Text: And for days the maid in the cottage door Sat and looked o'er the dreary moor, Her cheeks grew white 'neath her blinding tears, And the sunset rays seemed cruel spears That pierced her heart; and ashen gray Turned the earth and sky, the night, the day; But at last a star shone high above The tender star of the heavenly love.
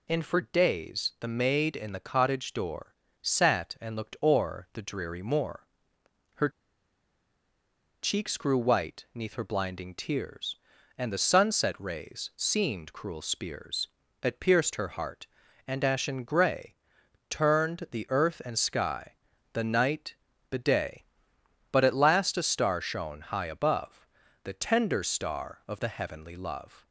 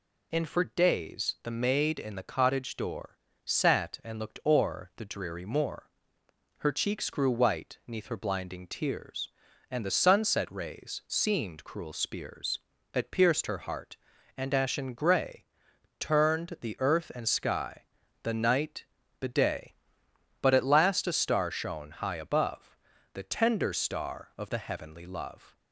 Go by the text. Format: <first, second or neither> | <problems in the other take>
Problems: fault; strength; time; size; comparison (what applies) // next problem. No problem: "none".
second | pauses between "door" and "Sat"; slight; at 2.9 s; 0.28 s long; slight in the second // pauses between "Her" and "cheeks"; strong; at 6.4 s; 1.5 s long // pauses between "gray" and "Turned"; noticeable; at 16.7 s; 0.54 s long; noticeable in the second // pauses between "above" and "The"; slight; at 24.0 s; 0.36 s long; slight in the second